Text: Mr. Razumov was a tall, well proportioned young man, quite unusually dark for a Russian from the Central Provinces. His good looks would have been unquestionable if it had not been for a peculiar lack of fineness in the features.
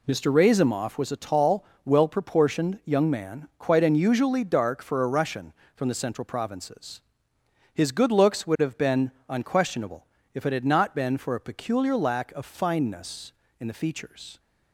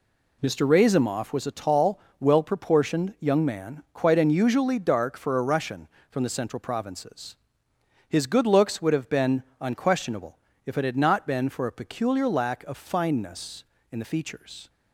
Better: neither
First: pauses between "been" and "unquestionable"; slight; at 9.1 s; 0.18 s long // pauses between "unquestionable" and "if"; slight; at 10.0 s; 0.26 s long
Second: pauses between "been" and "unquestionable"; slight; at 9.4 s; 0.18 s long // pauses between "unquestionable" and "if"; slight; at 10.3 s; 0.26 s long

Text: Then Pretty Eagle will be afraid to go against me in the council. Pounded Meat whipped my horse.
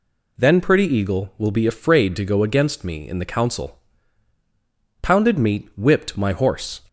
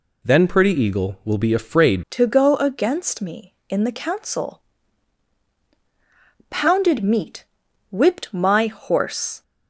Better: first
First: none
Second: changes voice at "to"; from 2.0 s on; 7.4 s long // pauses between "Meat" and "whipped"; noticeable; at 7.4 s; 0.46 s long

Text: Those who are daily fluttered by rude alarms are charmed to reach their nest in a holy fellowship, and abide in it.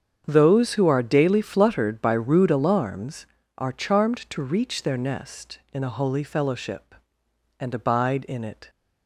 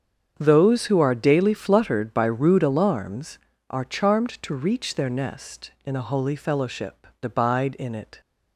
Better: first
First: starts louder than the rest; strong; until 1.2 s; 7.5 dB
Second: starts louder than the rest; strong; until 1.3 s; 7.5 dB // skips "and"; at 7.1 s

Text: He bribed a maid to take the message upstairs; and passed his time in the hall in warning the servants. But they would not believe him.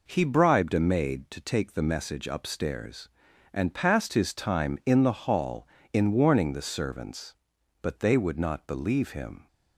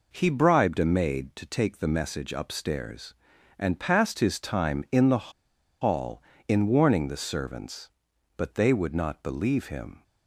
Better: first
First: none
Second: pauses between "the" and "hall"; noticeable; at 5.3 s; 0.49 s long

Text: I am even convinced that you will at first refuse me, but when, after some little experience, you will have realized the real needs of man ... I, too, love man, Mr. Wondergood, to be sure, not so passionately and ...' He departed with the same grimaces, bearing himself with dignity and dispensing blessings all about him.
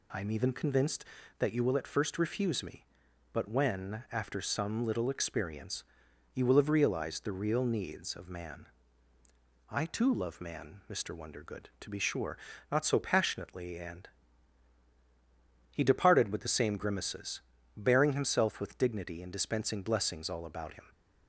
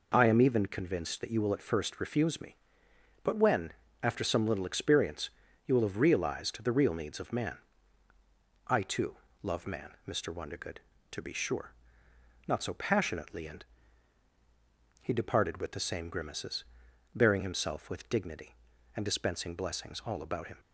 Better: neither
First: none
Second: none

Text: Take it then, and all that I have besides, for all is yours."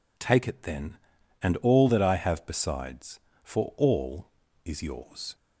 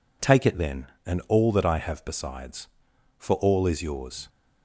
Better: neither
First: none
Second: none

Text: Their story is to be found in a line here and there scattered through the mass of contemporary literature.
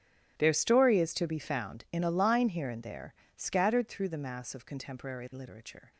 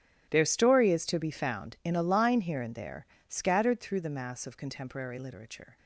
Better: neither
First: starts louder than the rest; strong; until 1.3 s; 11.5 dB // pauses between "there" and "scattered"; slight; at 3.1 s; 0.24 s long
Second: starts louder than the rest; strong; until 1.3 s; 11.5 dB // pauses between "there" and "scattered"; slight; at 3.0 s; 0.24 s long

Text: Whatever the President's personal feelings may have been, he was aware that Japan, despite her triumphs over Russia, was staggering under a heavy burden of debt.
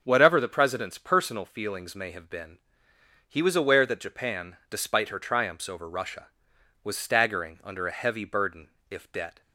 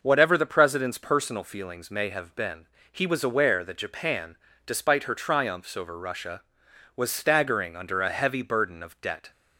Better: second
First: starts louder than the rest; until 1.0 s; 7 dB // says "if" for "of"; at 8.8 s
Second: none

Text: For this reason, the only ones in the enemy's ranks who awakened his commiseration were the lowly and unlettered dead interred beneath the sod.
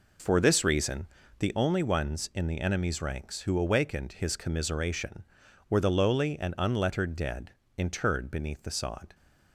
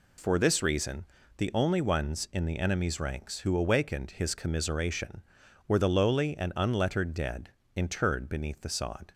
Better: second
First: starts louder than the rest; noticeable; until 1.6 s; 4.5 dB // pauses between "dead" and "interred"; slight; at 7.5 s; 0.26 s long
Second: pauses between "dead" and "interred"; slight; at 7.5 s; 0.26 s long

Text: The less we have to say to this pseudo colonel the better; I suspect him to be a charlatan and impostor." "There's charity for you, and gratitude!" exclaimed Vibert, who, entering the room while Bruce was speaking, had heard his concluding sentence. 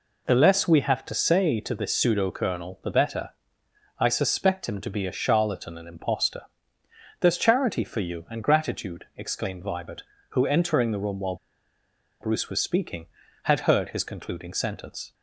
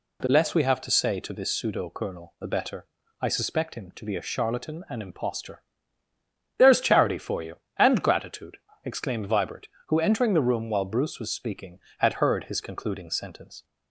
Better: second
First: pauses between "while" and "Bruce"; noticeable; at 11.3 s; 0.85 s long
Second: none

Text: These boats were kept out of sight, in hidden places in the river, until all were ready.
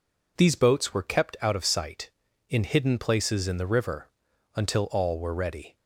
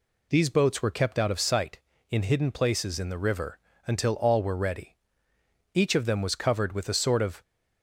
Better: first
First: none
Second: goes on to say "Each of them was covered with a sort of"; strong; from 5.7 s on; 1.7 s long

